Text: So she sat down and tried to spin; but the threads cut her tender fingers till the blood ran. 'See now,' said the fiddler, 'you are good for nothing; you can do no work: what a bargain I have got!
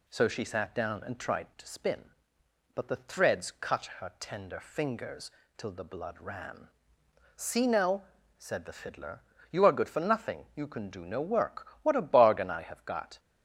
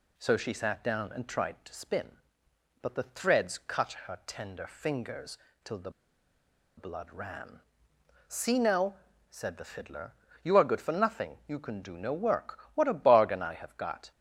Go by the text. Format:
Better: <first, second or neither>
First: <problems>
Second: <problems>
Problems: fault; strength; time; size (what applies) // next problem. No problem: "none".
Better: first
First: pauses between "fingers" and "till"; slight; at 5.2 s; 0.30 s long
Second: pauses between "fingers" and "till"; slight; at 5.3 s; 0.30 s long // pauses between "the" and "blood"; noticeable; at 5.8 s; 0.87 s long